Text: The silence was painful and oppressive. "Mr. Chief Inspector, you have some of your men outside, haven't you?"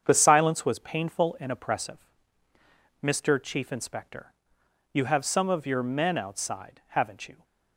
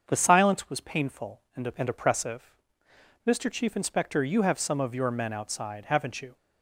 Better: first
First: starts louder than the rest; strong; until 1.0 s; 7.5 dB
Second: starts louder than the rest; until 1.0 s; 7 dB // says "and" twice; at 1.7 s

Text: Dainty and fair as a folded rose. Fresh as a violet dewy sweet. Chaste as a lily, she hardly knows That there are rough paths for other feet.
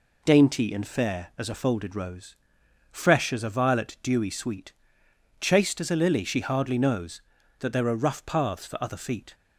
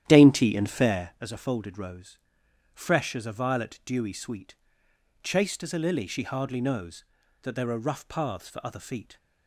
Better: first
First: none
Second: starts louder than the rest; strong; until 1.2 s; 11 dB

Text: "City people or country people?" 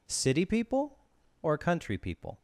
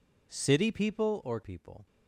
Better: first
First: none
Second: skips "country"; at 1.4 s

